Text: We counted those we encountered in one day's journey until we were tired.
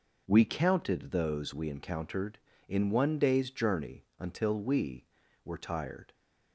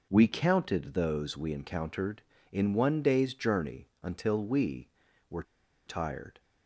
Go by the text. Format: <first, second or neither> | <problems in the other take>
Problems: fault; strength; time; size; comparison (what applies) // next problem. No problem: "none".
first | pauses between "were" and "tired"; at 5.4 s; 0.44 s long